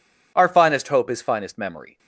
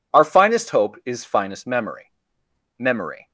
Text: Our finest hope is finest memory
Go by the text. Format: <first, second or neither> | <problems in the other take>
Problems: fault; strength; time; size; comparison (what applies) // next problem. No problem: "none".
first | says "memory" twice; at 2.7 s